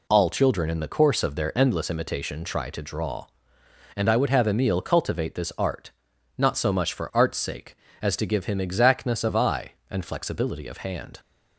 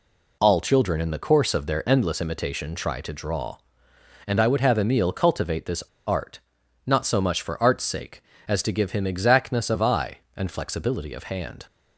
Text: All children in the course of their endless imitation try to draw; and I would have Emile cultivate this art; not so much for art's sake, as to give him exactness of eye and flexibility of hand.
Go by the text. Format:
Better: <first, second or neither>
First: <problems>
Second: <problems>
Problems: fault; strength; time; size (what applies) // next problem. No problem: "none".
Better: first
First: none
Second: pauses between "this" and "art"; slight; at 5.8 s; 0.24 s long